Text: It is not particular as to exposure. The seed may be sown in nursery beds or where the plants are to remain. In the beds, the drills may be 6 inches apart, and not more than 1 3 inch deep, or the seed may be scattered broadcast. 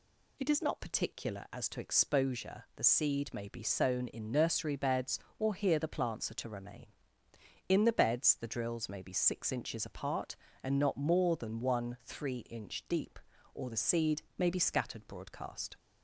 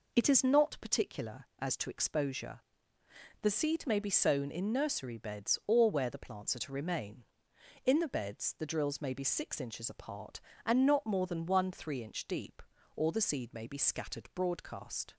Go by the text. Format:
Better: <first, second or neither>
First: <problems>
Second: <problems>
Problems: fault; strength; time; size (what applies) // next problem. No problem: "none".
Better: second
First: says "here" for "where"; at 5.5 s // pauses between "seed" and "may"; slight; at 14.2 s; 0.16 s long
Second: none